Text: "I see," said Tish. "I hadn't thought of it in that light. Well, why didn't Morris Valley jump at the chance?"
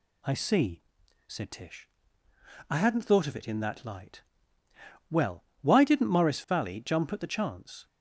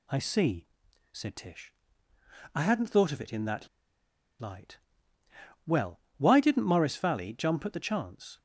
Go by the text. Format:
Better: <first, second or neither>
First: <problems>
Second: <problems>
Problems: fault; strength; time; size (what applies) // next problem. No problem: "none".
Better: first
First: none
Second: pauses between "that" and "light"; noticeable; at 3.6 s; 0.73 s long